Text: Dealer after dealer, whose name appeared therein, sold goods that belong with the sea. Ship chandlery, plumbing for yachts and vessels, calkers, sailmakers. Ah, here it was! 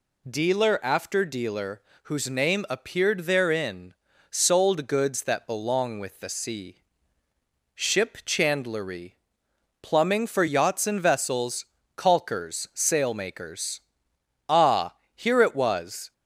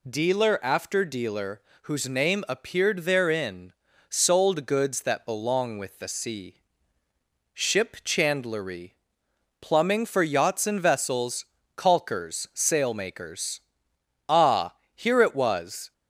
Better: neither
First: none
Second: none

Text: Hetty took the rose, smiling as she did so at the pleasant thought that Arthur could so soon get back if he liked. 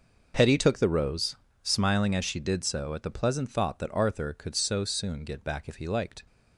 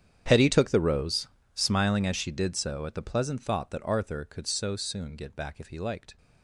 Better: first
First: none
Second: gets quieter; strong; throughout; 20 dB

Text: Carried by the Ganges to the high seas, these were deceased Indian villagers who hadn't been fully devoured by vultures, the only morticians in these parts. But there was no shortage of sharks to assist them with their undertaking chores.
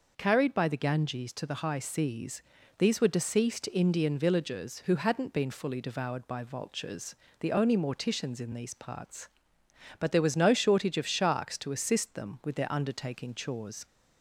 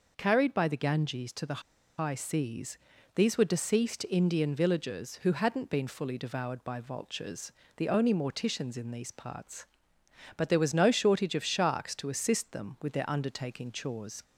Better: first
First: none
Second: pauses between "the" and "high"; at 1.6 s; 0.37 s long

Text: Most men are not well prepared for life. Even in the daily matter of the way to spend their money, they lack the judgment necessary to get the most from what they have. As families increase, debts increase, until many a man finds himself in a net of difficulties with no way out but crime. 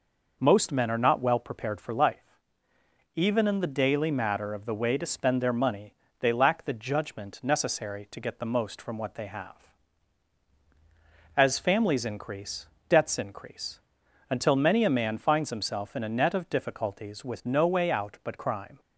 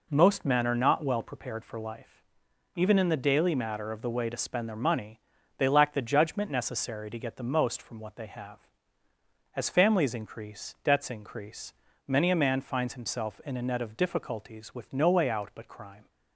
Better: first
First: none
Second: skips "until"; at 11.9 s

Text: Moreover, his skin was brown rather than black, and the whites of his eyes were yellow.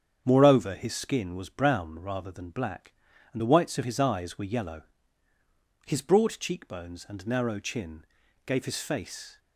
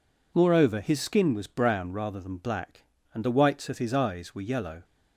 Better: second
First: starts louder than the rest; strong; until 1.2 s; 8 dB // goes on to say "His broad cheekbones and narrow chin gave his face"; strong; from 5.8 s on; 3.5 s long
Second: none

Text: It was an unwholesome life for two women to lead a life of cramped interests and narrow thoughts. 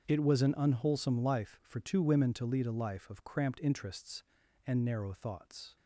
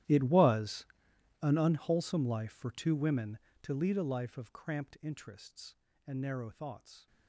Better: first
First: starts louder than the rest; until 1.1 s; 7 dB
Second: gets quieter; strong; throughout; 21 dB // starts louder than the rest; strong; until 1.6 s; 13.5 dB // pauses between "was" and "an"; noticeable; at 0.8 s; 0.56 s long

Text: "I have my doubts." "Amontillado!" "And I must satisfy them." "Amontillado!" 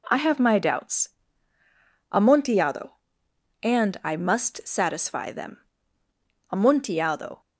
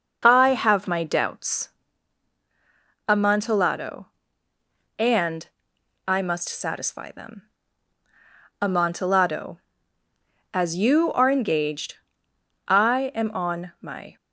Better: first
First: none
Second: starts louder than the rest; noticeable; until 1.2 s; 6 dB // pauses between "And" and "I"; noticeable; at 5.4 s; 0.58 s long // goes on to say "As you are engaged I am on my"; strong; from 10.5 s on; 3.6 s long

